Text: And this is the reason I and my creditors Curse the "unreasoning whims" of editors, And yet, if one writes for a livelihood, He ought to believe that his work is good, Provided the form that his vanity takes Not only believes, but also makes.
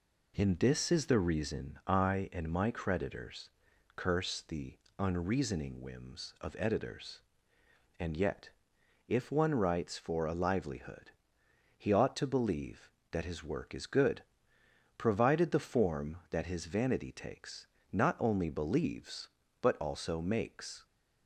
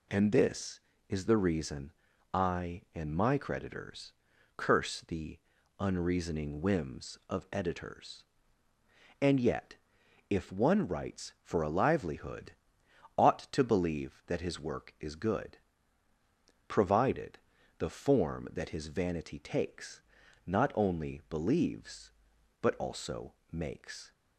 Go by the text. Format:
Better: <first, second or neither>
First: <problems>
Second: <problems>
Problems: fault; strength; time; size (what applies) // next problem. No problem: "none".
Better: first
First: pauses between "creditors" and "Curse"; at 3.5 s; 0.44 s long // pauses between "the" and "unreasoning"; slight; at 4.7 s; 0.22 s long // pauses between "takes" and "Not"; slight; at 17.6 s; 0.26 s long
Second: pauses between "reason" and "I"; at 1.9 s; 0.42 s long // pauses between "creditors" and "Curse"; noticeable; at 4.1 s; 0.46 s long // pauses between "the" and "unreasoning"; at 5.3 s; 0.40 s long // skips "He"; at 12.8 s // pauses between "Provided" and "the"; at 17.3 s; 0.40 s long // pauses between "takes" and "Not"; at 20.0 s; 0.44 s long // pauses between "also" and "makes"; slight; at 23.3 s; 0.18 s long